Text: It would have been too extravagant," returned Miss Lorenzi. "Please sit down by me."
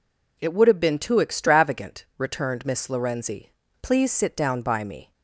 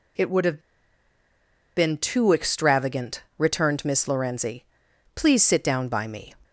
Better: first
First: none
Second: pauses between "have" and "been"; at 0.6 s; 1.1 s long

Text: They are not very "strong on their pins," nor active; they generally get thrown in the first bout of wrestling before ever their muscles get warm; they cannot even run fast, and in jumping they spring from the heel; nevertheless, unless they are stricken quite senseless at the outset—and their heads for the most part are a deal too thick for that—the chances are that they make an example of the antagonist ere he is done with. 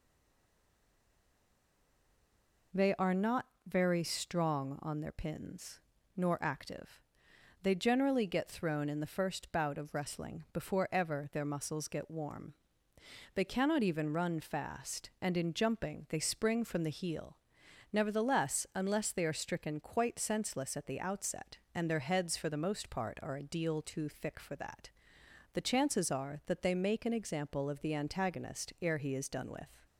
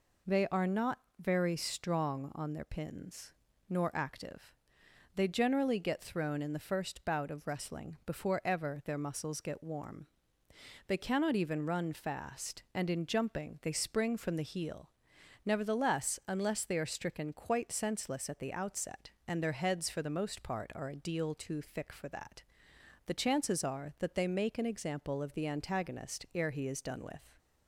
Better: second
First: stays silent before the first word; strong; until 2.7 s; 2.7 s long // pauses between "not" and "very"; slight; at 3.4 s; 0.20 s long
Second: pauses between "not" and "very"; slight; at 0.9 s; 0.20 s long

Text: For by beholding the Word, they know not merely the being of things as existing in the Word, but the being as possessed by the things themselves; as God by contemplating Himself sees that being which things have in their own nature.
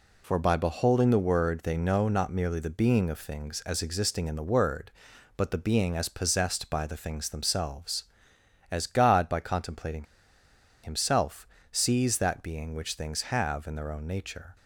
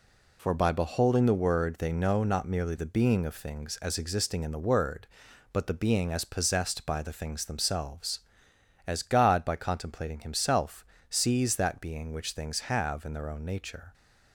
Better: second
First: pauses between "contemplating" and "Himself"; noticeable; at 10.0 s; 0.78 s long // pauses between "Himself" and "sees"; slight; at 11.4 s; 0.28 s long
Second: pauses between "Himself" and "sees"; slight; at 10.8 s; 0.28 s long

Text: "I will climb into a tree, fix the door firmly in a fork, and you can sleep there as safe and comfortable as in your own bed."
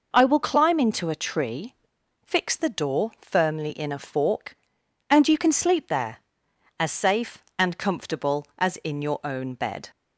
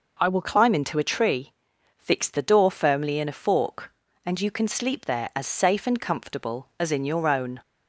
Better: first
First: none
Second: stops before "bed"; at 7.6 s

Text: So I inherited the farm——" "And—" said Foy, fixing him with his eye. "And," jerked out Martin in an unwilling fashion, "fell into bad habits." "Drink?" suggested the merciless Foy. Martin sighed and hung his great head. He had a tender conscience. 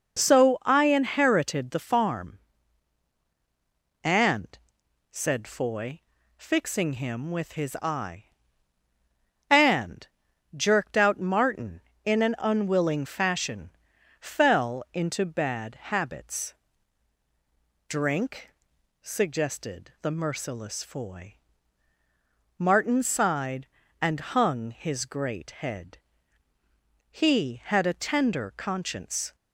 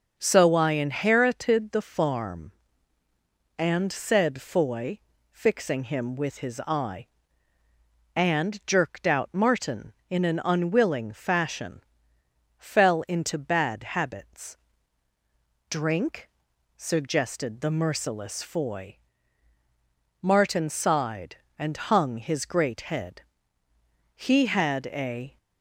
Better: first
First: none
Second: stops before "tender conscience"; at 25.3 s

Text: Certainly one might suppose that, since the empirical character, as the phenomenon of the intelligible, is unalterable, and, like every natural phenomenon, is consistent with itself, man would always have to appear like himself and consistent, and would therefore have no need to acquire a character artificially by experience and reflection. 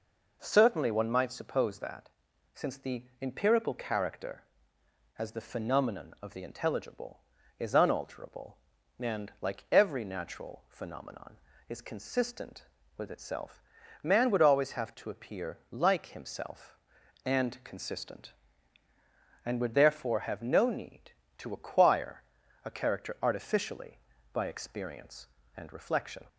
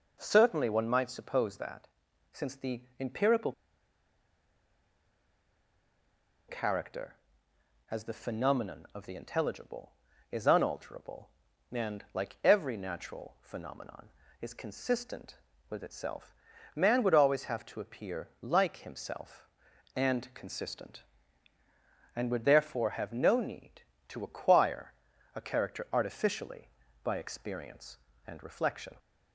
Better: first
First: pauses between "the" and "empirical"; slight; at 3.0 s; 0.18 s long // pauses between "acquire" and "a"; at 22.2 s; 0.44 s long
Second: pauses between "the" and "empirical"; slight; at 2.8 s; 0.18 s long // pauses between "empirical" and "character"; strong; at 3.5 s; 2.9 s long // pauses between "acquire" and "a"; at 24.9 s; 0.44 s long

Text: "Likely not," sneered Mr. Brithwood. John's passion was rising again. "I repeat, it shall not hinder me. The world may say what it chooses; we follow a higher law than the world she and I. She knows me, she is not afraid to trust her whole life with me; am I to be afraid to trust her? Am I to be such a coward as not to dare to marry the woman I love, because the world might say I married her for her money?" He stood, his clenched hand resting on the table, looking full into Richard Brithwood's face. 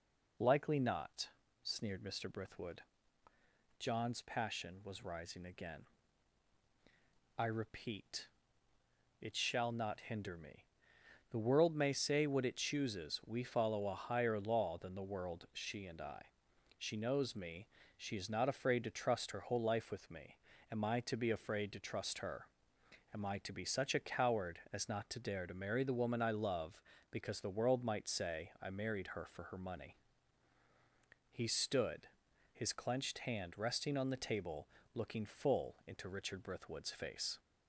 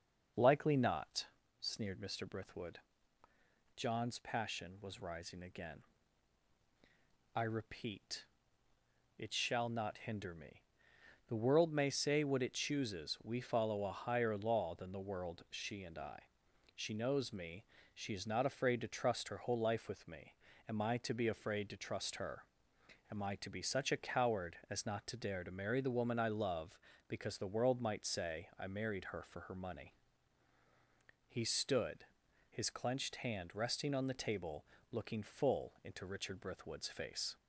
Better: first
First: none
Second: starts louder than the rest; noticeable; until 1.4 s; 6 dB

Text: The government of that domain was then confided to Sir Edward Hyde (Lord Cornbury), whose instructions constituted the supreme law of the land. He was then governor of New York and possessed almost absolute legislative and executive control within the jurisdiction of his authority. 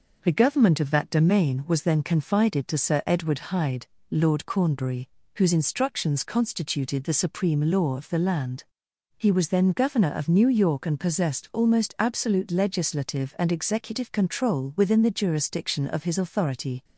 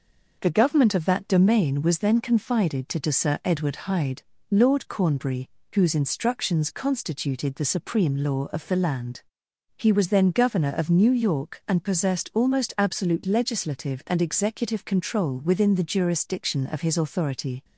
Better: first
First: none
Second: says "to" twice; at 3.0 s

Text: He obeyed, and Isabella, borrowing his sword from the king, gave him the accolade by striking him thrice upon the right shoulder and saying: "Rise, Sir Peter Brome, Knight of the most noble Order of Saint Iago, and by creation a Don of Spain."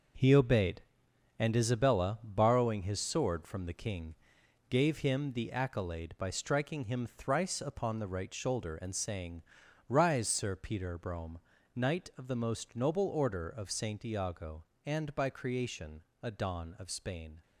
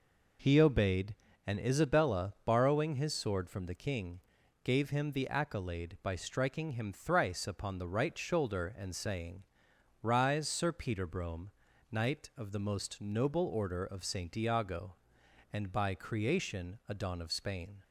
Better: second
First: gets quieter; strong; throughout; 8.5 dB // pauses between "creation" and "a"; slight; at 16.0 s; 0.20 s long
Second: none

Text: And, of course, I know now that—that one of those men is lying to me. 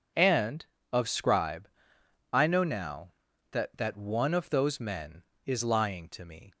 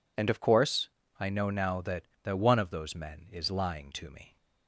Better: second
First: says "scribe" for "course"; at 1.0 s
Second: none

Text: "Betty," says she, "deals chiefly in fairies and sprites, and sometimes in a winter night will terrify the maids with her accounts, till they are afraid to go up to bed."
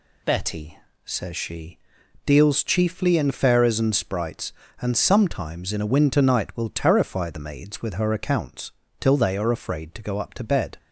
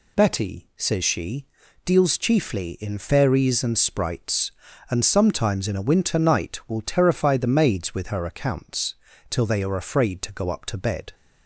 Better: neither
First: none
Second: none

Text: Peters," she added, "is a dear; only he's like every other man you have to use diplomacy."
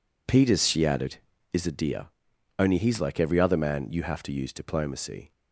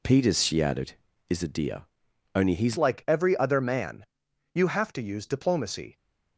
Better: first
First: none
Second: changes voice at "like"; from 2.7 s on; 3.2 s long // pauses between "man" and "you"; noticeable; at 4.0 s; 0.48 s long

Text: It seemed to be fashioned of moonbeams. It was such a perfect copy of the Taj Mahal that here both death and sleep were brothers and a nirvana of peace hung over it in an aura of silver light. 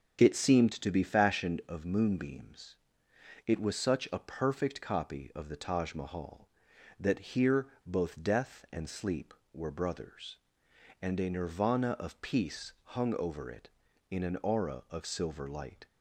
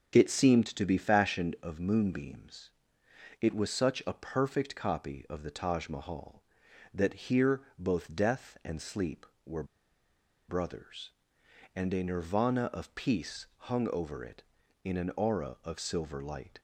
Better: first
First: starts louder than the rest; until 1.2 s; 7 dB // pauses between "here" and "both"; slight; at 7.6 s; 0.20 s long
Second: starts louder than the rest; until 1.1 s; 6.5 dB // pauses between "here" and "both"; slight; at 7.6 s; 0.18 s long // pauses between "were" and "brothers"; noticeable; at 9.6 s; 0.84 s long

